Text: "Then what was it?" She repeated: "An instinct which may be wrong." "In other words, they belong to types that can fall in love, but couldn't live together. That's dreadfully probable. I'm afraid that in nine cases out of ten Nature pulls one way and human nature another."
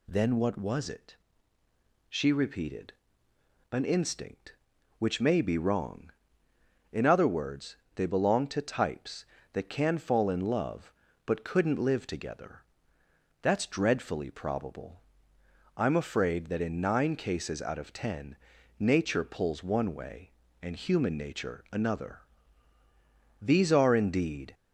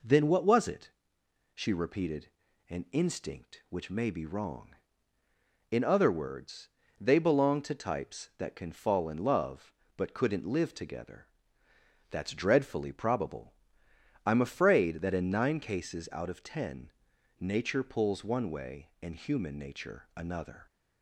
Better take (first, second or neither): second